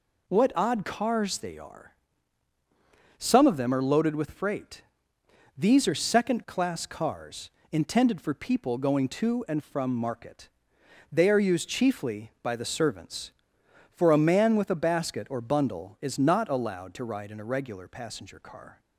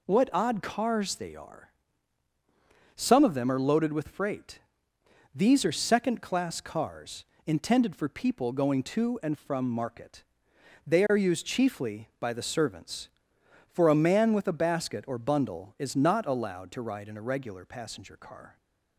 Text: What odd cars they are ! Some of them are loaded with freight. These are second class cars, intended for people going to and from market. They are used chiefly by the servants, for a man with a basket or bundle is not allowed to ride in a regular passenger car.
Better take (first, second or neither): neither